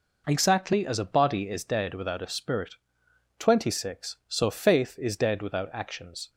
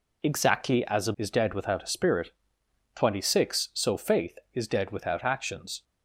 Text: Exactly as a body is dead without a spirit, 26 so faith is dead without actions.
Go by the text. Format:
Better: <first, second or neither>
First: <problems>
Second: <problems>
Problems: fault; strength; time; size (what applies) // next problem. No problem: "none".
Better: first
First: none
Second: skips "body"; at 1.1 s